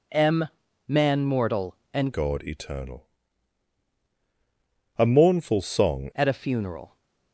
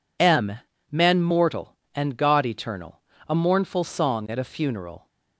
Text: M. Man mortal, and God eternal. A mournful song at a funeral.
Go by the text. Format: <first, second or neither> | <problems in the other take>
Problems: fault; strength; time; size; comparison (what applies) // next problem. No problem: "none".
second | changes voice from "God" to "song"; from 2.1 to 6.1 s; 4.0 s long